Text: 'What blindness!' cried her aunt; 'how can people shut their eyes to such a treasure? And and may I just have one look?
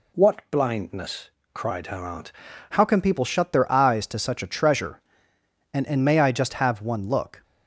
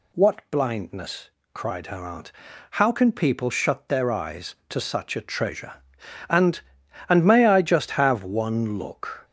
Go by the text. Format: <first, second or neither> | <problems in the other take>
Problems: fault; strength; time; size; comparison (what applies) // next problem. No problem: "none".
second | changes voice at "how"; from 2.6 s on; 4.8 s long